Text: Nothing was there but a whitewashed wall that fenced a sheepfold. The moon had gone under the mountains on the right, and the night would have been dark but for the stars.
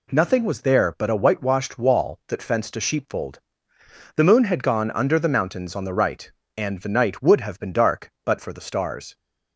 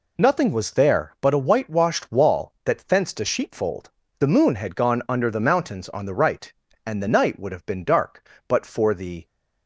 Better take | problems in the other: first | stops before "stars"; at 9.2 s

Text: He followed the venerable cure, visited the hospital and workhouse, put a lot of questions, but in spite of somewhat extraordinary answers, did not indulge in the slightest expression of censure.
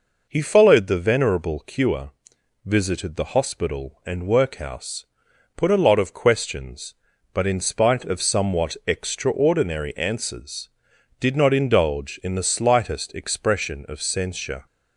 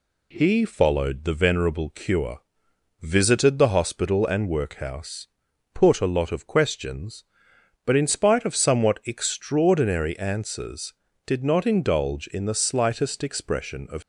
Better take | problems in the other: first | stops before "censure"; at 14.0 s

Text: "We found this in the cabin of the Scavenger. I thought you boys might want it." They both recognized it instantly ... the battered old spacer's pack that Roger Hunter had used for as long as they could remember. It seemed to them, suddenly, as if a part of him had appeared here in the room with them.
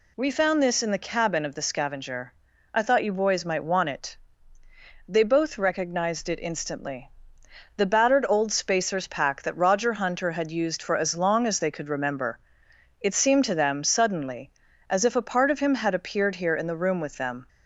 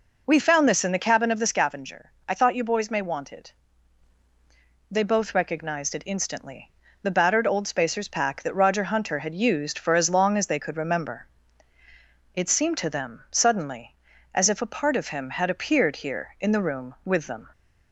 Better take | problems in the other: first | says "may" for "might"; at 2.8 s

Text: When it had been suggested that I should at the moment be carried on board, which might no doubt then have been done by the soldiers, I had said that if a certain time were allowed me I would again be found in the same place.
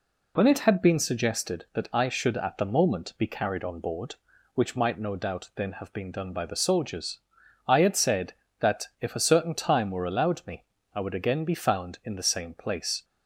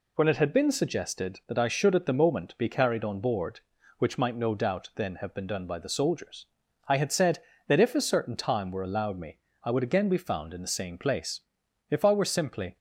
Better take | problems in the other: first | pauses between "me" and "I"; slight; at 9.3 s; 0.26 s long; slight in the first // goes on to say "If I were simply"; noticeable; from 11.8 s on; 0.88 s long

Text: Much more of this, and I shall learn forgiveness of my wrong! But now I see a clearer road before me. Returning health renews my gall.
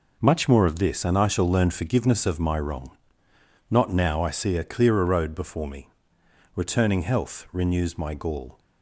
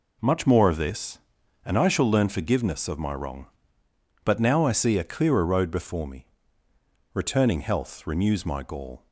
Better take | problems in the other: second | says "Not" for "But"; at 3.7 s

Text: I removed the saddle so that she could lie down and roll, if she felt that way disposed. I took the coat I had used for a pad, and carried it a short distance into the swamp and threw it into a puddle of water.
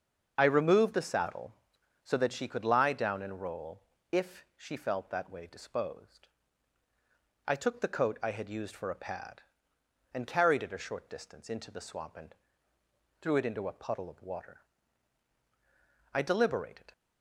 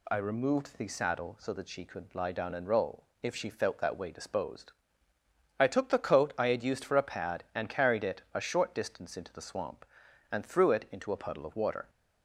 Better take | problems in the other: second | starts louder than the rest; until 1.3 s; 7 dB // pauses between "and" and "threw"; noticeable; at 12.3 s; 0.88 s long // goes on to say "I deliberated"; noticeable; from 16.1 s on; 0.78 s long

